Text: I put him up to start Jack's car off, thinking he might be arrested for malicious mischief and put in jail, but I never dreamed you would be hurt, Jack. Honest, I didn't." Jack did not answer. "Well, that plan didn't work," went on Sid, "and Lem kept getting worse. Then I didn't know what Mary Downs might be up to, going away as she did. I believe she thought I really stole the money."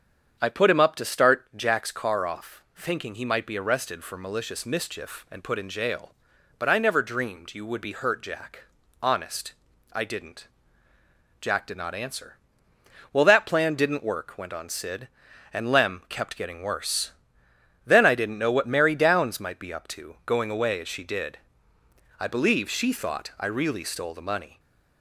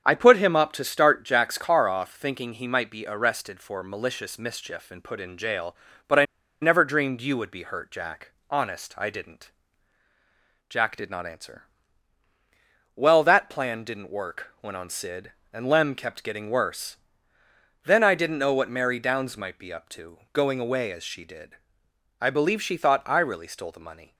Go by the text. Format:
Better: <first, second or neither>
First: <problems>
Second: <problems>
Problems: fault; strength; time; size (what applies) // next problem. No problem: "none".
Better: first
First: starts louder than the rest; strong; until 1.4 s; 7.5 dB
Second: starts louder than the rest; strong; until 1.0 s; 7.5 dB // pauses between "I" and "never"; at 6.2 s; 0.36 s long